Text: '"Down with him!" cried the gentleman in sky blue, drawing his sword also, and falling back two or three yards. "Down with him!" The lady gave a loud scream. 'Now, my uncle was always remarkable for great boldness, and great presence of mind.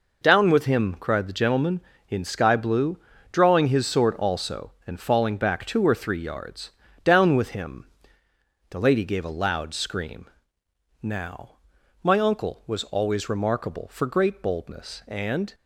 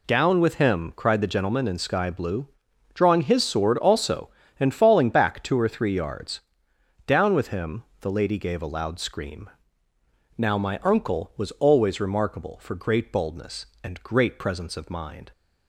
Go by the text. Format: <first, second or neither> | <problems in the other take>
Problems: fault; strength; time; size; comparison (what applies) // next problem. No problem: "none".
second | stops before "great presence of mind"; at 15.5 s